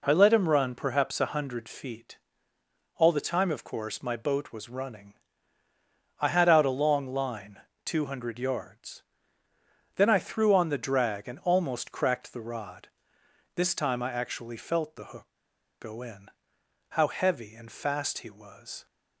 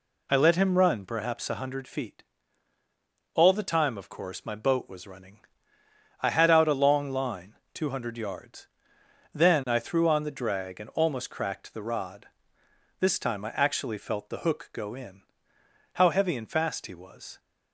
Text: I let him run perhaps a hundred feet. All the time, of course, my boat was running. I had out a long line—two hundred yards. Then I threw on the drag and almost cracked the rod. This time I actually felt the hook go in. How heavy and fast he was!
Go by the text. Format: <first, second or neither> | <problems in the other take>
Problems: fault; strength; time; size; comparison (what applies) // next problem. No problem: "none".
second | pauses between "hook" and "go"; noticeable; at 15.2 s; 0.55 s long